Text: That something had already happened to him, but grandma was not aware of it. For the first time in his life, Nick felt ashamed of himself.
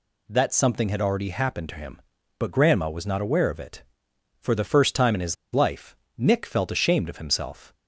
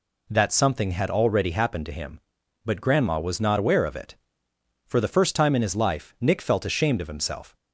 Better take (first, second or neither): second